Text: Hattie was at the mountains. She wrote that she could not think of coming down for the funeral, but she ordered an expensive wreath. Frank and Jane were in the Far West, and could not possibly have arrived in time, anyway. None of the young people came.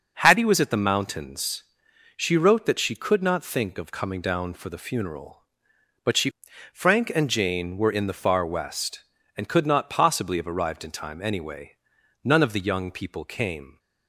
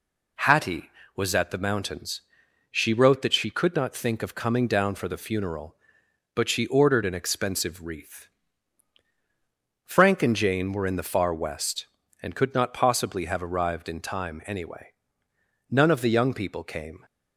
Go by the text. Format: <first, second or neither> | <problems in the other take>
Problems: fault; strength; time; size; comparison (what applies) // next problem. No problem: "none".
second | skips "ordered an expensive wreath"; at 6.5 s